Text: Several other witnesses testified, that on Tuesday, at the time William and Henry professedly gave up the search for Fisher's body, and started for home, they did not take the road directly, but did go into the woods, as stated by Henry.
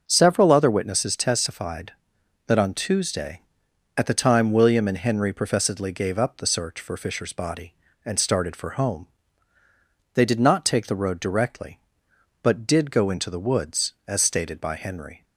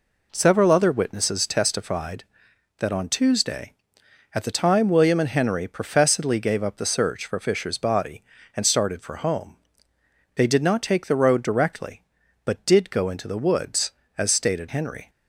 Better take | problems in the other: first | skips "by"; at 14.6 s

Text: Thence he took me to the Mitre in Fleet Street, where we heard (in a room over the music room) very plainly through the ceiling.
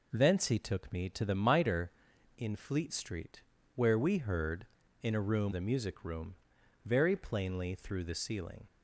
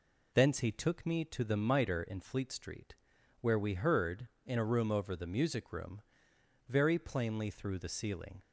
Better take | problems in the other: second | skips "over"; at 5.5 s

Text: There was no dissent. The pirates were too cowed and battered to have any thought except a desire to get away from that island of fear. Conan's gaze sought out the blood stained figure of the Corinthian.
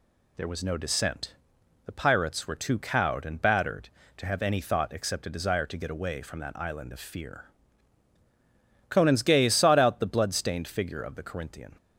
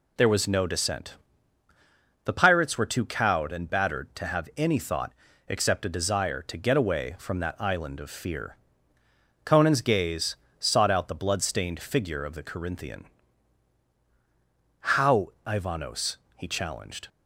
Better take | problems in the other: first | pauses between "thought" and "except"; slight; at 5.1 s; 0.36 s long // pauses between "gaze" and "sought"; slight; at 10.3 s; 0.22 s long // goes on to say "How Ivanos he challenged"; strong; from 14.8 s on; 2.2 s long

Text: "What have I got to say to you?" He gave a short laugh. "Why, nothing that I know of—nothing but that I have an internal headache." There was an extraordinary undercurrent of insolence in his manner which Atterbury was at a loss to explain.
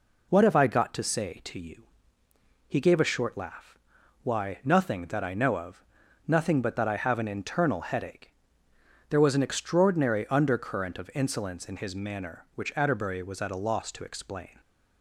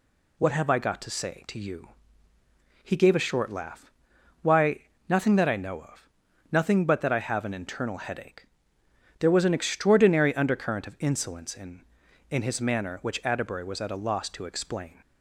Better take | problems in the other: first | says "in" twice; at 12.3 s

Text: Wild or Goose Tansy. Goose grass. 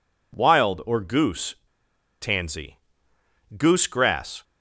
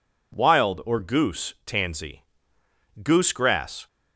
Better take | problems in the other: second | pauses between "Goose" and "Tansy"; noticeable; at 1.5 s; 0.67 s long

